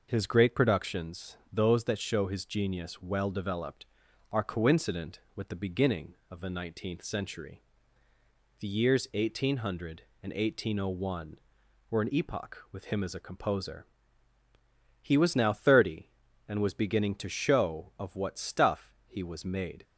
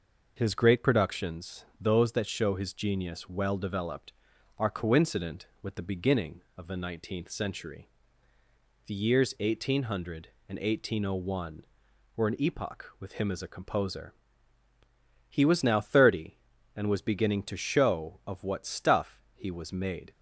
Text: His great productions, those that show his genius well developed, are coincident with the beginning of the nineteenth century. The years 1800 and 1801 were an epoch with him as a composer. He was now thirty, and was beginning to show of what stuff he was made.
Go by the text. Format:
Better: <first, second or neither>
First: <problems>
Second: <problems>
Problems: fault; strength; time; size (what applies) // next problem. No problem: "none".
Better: neither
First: none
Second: none